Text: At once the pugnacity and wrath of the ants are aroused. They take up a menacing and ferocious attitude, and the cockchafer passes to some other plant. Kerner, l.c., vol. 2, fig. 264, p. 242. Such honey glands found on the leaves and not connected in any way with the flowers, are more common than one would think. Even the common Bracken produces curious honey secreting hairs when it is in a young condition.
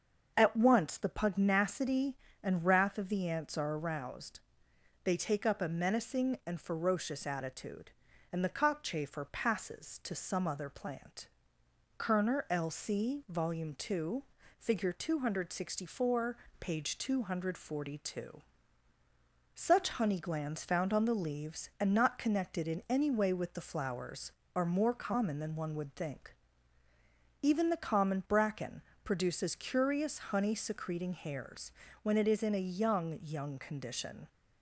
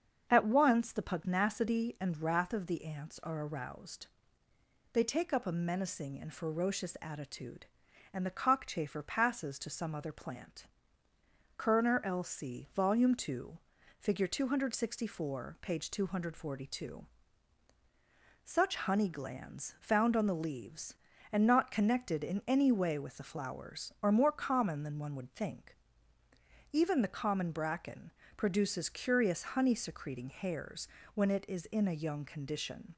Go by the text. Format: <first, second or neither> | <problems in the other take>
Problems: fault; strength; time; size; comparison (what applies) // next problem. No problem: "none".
second | starts louder than the rest; until 1.3 s; 6.5 dB; also in the second // pauses between "Bracken" and "produces"; slight; at 28.8 s; 0.22 s long; slight in the second // pauses between "hairs" and "when"; slight; at 31.7 s; 0.32 s long; slight in the second // says "young" twice; at 33.2 s